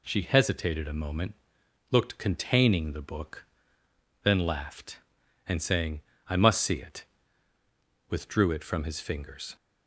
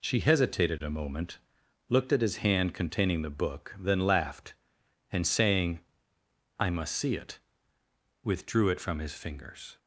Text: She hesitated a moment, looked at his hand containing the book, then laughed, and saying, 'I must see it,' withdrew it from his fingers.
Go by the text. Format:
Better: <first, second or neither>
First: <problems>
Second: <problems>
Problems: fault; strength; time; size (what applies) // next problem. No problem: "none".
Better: second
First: skips "at his hand"; at 2.1 s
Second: none